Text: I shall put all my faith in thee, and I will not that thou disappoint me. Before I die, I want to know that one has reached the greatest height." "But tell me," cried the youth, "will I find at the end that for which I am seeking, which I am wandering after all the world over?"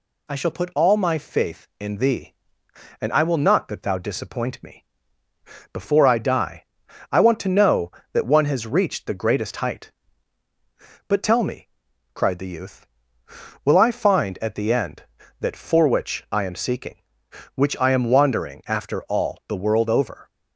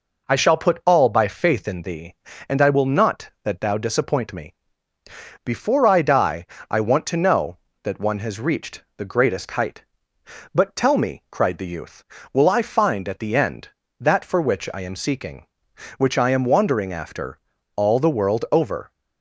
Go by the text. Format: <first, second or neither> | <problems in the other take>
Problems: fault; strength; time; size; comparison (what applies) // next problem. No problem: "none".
first | says "by" for "my"; at 1.0 s // pauses between "after" and "all"; at 17.3 s; 0.39 s long